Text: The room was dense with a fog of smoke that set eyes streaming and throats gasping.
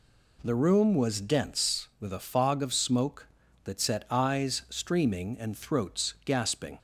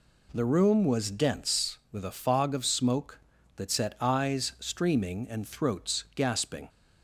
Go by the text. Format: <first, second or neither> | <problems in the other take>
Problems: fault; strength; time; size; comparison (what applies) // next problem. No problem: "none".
neither | none